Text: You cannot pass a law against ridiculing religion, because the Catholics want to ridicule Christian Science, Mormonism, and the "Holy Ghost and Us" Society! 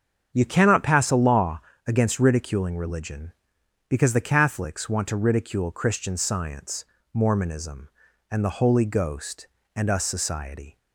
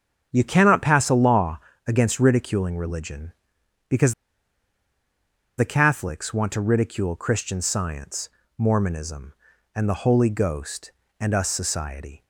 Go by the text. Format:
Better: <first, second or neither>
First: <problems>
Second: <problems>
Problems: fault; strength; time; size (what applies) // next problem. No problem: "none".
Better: first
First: starts louder than the rest; strong; until 1.3 s; 7.5 dB // pauses between "law" and "against"; slight; at 1.6 s; 0.24 s long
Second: starts louder than the rest; strong; until 1.3 s; 7.5 dB // pauses between "law" and "against"; slight; at 1.5 s; 0.26 s long // pauses between "because" and "the"; strong; at 4.1 s; 1.4 s long